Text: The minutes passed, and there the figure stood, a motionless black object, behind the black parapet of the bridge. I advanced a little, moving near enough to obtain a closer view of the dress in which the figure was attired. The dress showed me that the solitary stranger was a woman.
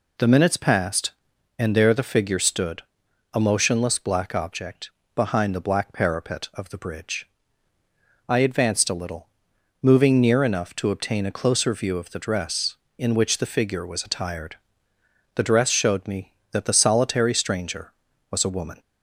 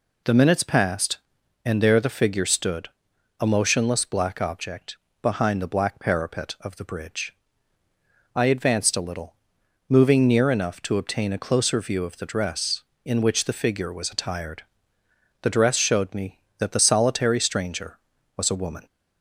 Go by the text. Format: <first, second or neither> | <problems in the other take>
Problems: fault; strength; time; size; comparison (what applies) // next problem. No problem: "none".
neither | none